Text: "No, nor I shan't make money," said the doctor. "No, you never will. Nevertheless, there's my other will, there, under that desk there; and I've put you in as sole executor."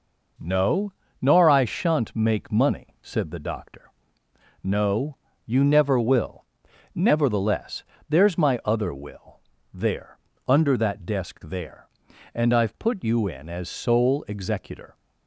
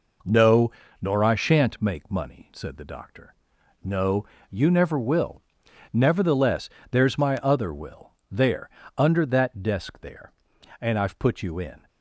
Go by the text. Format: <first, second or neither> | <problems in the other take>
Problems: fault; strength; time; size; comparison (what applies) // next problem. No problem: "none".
first | stops before "as sole executor"; at 11.8 s